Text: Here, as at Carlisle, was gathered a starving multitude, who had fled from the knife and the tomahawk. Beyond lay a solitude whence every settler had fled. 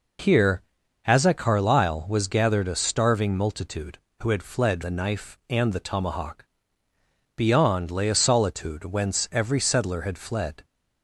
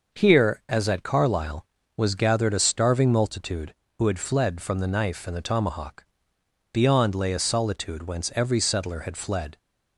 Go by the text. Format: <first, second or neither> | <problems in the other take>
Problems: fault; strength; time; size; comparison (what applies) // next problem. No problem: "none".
second | skips "from"; at 4.8 s